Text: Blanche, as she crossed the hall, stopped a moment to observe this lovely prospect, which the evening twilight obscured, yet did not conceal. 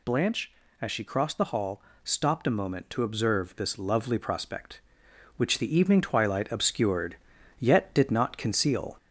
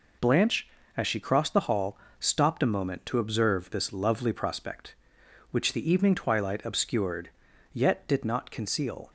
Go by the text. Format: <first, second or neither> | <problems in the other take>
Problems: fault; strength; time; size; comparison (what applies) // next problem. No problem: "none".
second | gets louder; slight; throughout; 3 dB